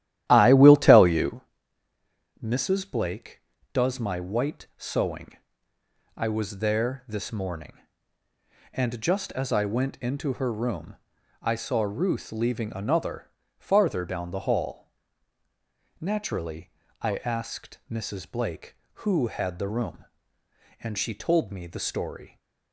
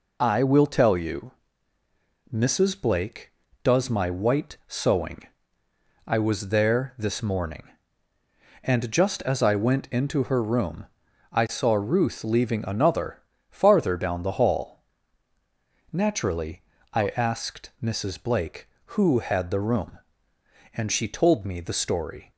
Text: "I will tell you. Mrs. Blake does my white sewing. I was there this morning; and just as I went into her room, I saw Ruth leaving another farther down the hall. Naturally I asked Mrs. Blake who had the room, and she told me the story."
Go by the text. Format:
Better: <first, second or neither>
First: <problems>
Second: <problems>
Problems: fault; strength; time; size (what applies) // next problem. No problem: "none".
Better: second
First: starts louder than the rest; strong; until 1.5 s; 12.5 dB // pauses between "another" and "farther"; slight; at 13.2 s; 0.30 s long // pauses between "Naturally" and "I"; slight; at 16.7 s; 0.32 s long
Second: pauses between "another" and "farther"; slight; at 13.2 s; 0.30 s long // pauses between "Naturally" and "I"; slight; at 16.6 s; 0.32 s long